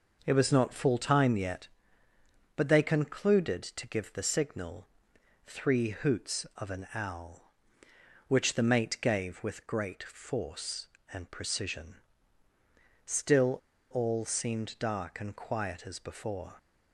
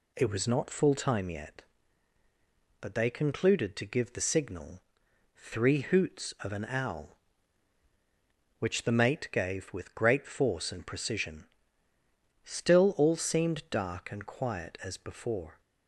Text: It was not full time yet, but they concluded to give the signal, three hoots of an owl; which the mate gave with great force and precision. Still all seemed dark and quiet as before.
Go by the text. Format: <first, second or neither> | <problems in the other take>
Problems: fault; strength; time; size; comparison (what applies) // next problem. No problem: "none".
second | pauses between "Still" and "all"; slight; at 13.5 s; 0.32 s long